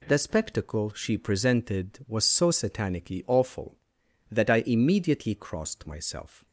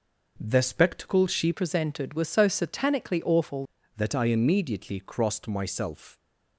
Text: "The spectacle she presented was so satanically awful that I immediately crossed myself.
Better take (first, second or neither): first